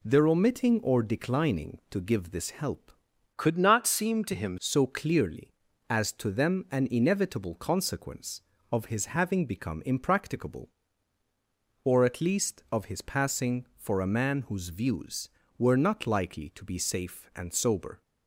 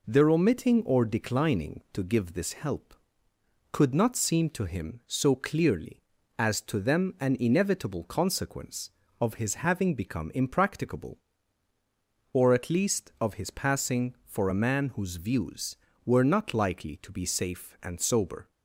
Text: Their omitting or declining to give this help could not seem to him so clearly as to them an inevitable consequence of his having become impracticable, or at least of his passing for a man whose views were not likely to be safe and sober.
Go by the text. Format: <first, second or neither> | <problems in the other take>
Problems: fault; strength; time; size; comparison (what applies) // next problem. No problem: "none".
second | changes voice from "could" to "him"; from 3.3 to 4.5 s; 1.2 s long